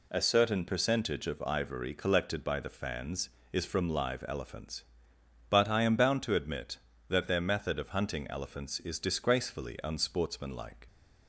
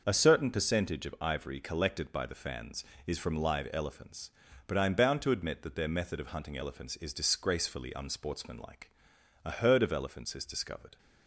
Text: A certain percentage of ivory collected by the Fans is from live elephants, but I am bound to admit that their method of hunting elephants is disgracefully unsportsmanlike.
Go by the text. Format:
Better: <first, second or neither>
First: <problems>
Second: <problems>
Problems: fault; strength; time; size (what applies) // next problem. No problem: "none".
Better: first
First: none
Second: starts louder than the rest; noticeable; until 1.0 s; 6 dB // goes on to say "A herd of elephants is discovered"; from 9.4 s on; 1.5 s long